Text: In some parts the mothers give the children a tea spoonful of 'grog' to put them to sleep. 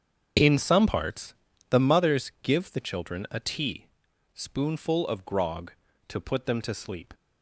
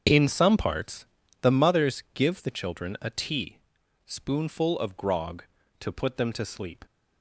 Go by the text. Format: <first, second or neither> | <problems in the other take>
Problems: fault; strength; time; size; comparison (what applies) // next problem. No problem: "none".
neither | starts louder than the rest; strong; the same in both // pauses between "parts" and "the"; the same in both // pauses between "tea" and "spoonful"; noticeable; the same in both